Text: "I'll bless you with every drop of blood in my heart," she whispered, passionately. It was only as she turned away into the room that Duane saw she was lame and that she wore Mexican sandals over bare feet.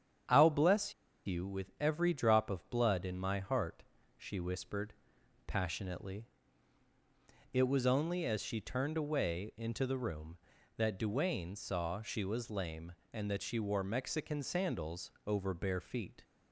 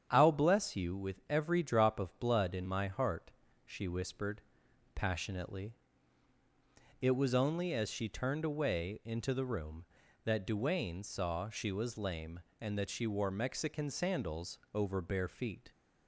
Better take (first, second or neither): second